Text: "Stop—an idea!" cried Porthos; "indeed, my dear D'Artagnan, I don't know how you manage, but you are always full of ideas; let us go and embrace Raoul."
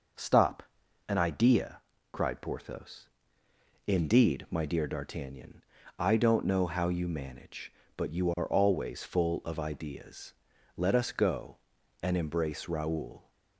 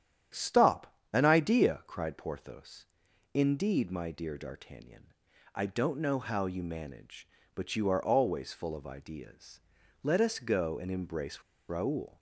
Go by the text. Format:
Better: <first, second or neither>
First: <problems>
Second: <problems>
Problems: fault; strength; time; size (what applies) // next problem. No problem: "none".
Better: first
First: none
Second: starts louder than the rest; strong; until 1.5 s; 10 dB // pauses between "embrace" and "Raoul"; slight; at 11.4 s; 0.26 s long